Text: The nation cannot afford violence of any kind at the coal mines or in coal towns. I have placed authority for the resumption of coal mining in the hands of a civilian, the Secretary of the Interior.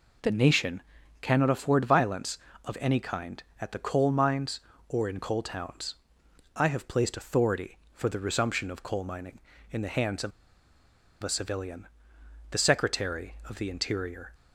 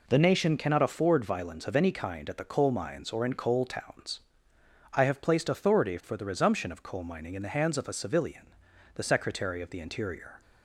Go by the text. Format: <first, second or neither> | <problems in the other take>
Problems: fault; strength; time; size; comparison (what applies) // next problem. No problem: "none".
second | pauses between "nation" and "cannot"; at 0.8 s; 0.40 s long // pauses between "of" and "a"; noticeable; at 10.3 s; 0.93 s long